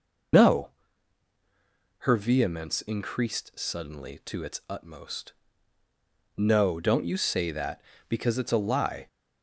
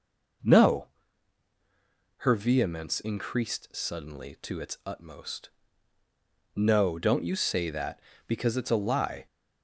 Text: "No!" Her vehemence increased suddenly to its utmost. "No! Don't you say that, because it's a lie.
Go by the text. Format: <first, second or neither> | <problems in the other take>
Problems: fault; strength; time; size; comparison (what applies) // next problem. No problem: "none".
second | loses the start of "No"; at 0.3 s; 90 ms